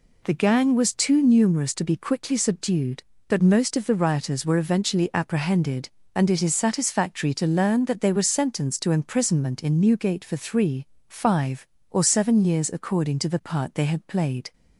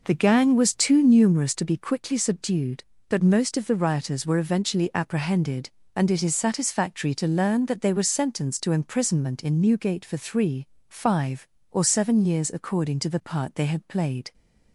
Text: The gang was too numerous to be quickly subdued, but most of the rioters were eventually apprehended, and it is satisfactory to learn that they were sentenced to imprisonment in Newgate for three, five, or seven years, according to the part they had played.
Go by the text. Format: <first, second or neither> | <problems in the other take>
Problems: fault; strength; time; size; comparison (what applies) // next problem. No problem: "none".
first | starts louder than the rest; noticeable; until 1.7 s; 5 dB